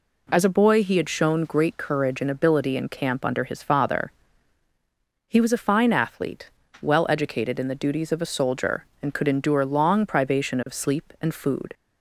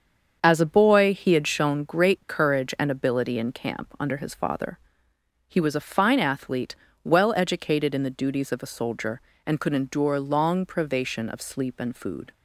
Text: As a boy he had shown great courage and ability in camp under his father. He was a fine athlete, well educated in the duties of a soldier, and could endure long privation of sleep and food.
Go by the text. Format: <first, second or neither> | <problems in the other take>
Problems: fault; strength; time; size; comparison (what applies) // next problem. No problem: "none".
first | starts louder than the rest; strong; until 1.7 s; 7 dB